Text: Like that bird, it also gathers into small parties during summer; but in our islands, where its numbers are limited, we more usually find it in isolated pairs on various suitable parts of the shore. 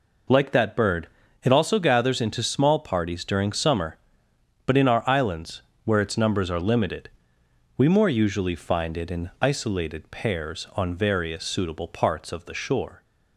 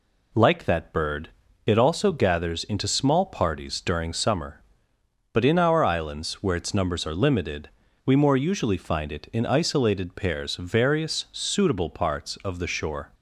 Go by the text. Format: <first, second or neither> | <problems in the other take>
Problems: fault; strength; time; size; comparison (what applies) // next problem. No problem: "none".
first | skips "on"; at 10.5 s